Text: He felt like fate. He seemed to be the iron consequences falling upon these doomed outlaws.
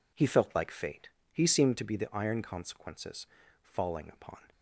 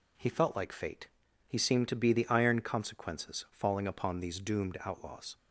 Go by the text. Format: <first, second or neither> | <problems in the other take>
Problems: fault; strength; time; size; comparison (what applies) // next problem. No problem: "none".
second | pauses between "consequences" and "falling"; at 3.2 s; 0.38 s long // stops before "these doomed outlaws"; at 4.5 s